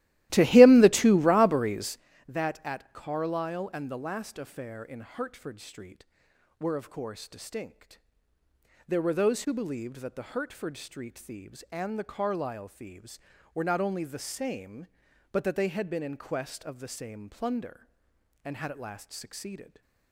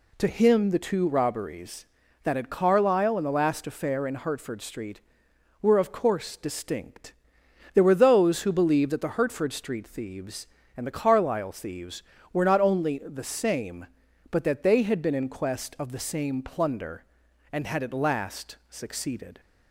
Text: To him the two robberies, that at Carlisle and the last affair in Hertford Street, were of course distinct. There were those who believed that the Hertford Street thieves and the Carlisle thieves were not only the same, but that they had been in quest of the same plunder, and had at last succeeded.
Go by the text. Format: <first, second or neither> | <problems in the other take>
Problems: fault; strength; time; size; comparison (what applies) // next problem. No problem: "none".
second | starts louder than the rest; strong; until 2.1 s; 16 dB